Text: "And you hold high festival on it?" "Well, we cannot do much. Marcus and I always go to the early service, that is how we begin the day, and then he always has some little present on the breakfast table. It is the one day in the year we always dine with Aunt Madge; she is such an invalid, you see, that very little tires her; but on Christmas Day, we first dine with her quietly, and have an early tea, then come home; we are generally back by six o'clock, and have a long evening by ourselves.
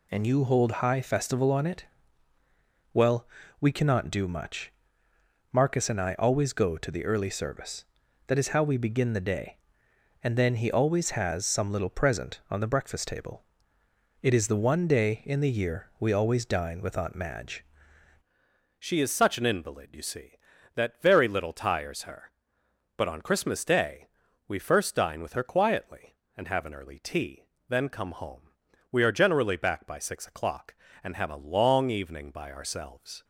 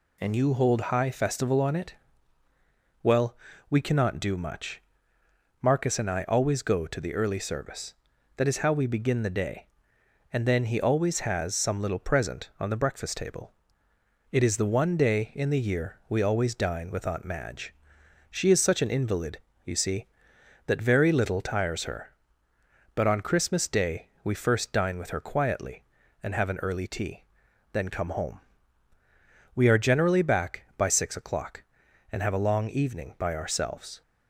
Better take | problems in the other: second | changes voice at "she"; from 18.7 s on; 14.5 s long

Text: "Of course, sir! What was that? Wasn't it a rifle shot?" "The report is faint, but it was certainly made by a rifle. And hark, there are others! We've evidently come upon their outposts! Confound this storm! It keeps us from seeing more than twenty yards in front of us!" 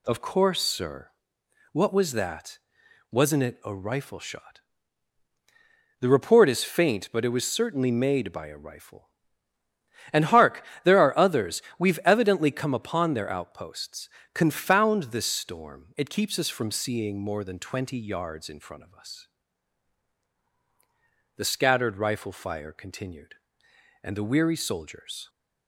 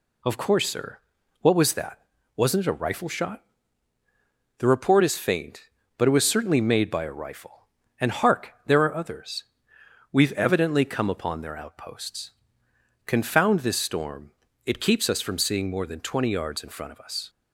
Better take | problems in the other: second | goes on to say "The scattered rifle fire continued and the weary soldiers"; strong; from 21.3 s on; 3.9 s long

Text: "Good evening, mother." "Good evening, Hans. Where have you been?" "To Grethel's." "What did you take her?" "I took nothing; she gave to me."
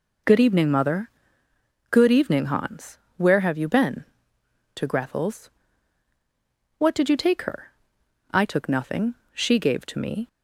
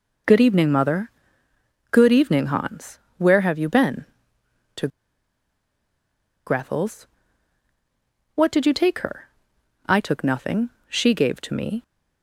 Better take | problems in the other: first | pauses between "To" and "Grethel's"; strong; at 4.8 s; 1.5 s long

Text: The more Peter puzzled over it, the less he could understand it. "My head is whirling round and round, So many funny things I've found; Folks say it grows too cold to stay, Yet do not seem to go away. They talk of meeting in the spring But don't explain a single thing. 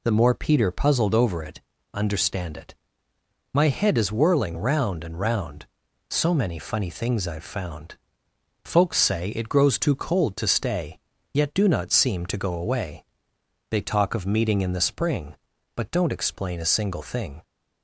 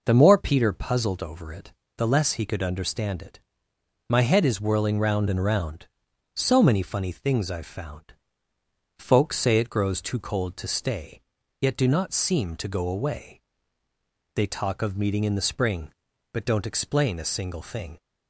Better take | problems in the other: second | skips "the less he could"; at 1.7 s

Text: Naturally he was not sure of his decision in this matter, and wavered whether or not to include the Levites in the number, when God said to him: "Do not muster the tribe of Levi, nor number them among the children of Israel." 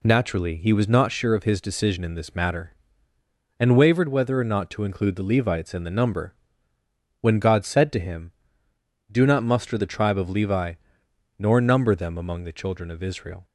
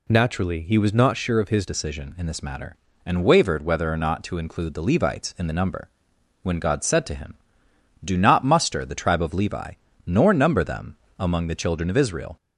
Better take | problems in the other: first | changes voice at "decision"; from 1.6 s on; 10.7 s long // pauses between "them" and "among"; slight; at 10.9 s; 0.24 s long

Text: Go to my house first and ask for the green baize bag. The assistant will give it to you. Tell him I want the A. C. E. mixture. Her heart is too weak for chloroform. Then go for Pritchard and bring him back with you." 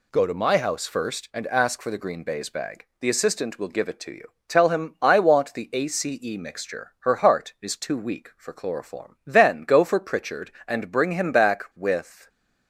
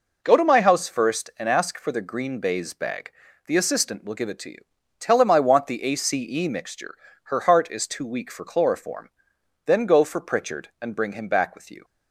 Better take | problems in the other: second | stops before "you"; at 12.2 s

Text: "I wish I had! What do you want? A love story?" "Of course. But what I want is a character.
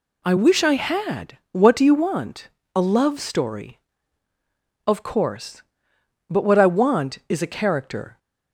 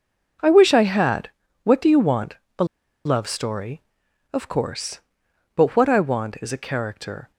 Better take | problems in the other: first | pauses between "A" and "love"; at 2.6 s; 0.40 s long

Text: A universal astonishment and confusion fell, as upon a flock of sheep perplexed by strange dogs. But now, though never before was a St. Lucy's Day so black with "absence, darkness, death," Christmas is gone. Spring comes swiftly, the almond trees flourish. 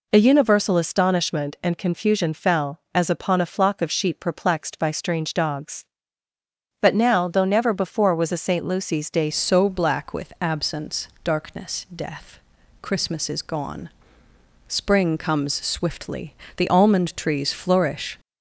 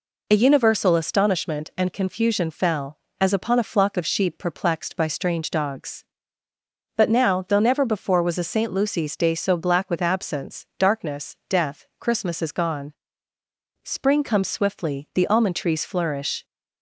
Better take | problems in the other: second | changes voice at "so"; from 9.3 s on; 8.8 s long

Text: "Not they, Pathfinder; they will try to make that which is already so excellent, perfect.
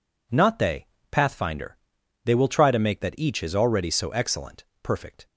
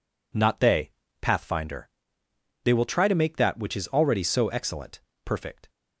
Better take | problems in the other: second | says "each" for "which"; at 3.1 s

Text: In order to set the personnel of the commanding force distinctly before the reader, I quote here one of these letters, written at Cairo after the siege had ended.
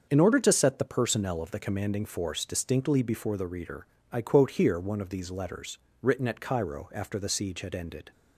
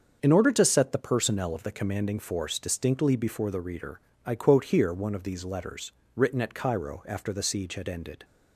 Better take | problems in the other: neither | starts louder than the rest; the same in both

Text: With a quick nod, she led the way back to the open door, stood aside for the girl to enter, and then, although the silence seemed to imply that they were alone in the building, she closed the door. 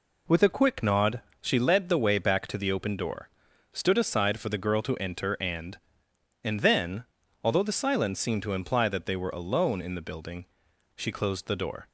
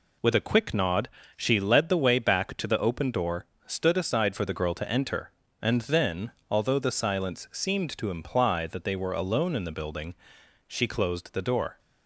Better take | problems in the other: second | says "and" twice; at 6.4 s

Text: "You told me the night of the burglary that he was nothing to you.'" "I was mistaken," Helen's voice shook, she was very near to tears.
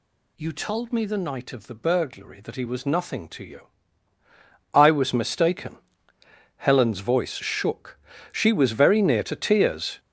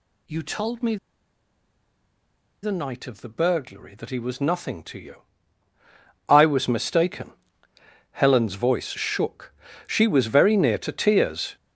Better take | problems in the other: first | pauses between "me" and "the"; strong; at 0.9 s; 1.6 s long

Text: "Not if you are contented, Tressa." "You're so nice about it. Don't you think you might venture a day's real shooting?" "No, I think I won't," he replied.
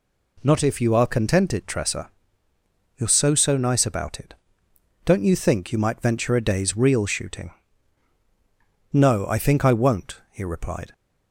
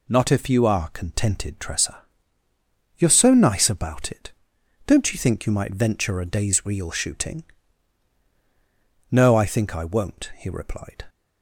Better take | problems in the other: second | says "so" twice; at 3.3 s

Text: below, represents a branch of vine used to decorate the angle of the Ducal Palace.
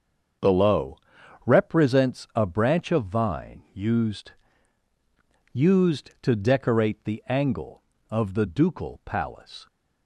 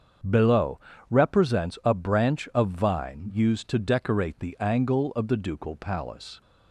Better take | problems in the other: second | starts louder than the rest; until 1.9 s; 7 dB; strong in the second // says "used" twice; at 5.5 s

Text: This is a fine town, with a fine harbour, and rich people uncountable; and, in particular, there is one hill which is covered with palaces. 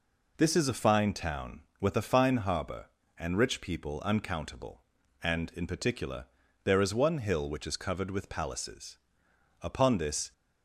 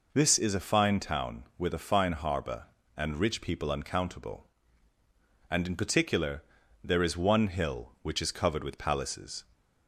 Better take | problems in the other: second | goes on to say "Upon this"; noticeable; from 9.6 s on; 0.70 s long

